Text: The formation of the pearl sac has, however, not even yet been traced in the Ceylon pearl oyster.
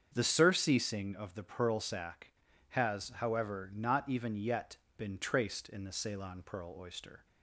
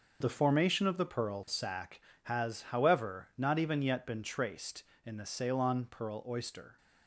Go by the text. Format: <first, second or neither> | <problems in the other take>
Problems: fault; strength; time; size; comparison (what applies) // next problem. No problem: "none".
second | starts louder than the rest; strong; until 1.1 s; 7.5 dB // says "surceasing" for "formation"; at 0.2 s // pauses between "yet" and "been"; slight; at 4.7 s; 0.18 s long